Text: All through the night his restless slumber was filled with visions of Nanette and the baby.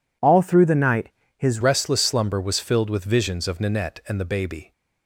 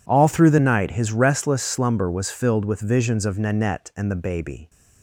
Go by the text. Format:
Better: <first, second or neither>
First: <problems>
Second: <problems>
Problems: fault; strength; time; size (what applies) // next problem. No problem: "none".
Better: second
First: pauses between "night" and "his"; slight; at 1.0 s; 0.28 s long // changes voice at "restless"; from 1.6 s on; 3.1 s long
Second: none